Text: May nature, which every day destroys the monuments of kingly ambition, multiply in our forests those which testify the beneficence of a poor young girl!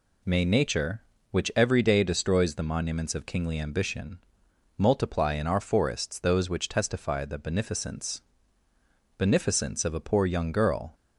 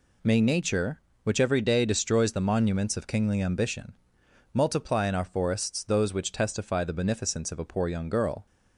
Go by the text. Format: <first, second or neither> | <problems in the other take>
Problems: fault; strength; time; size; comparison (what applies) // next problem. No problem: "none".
second | says "beneficence" twice; at 9.1 s